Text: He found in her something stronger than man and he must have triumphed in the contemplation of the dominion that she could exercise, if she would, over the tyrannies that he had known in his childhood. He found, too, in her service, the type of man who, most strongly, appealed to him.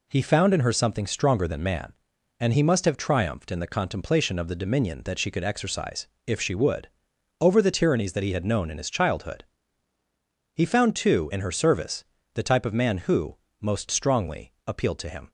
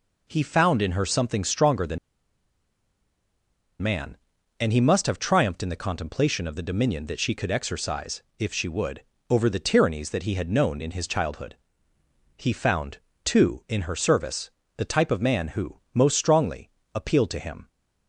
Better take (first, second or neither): first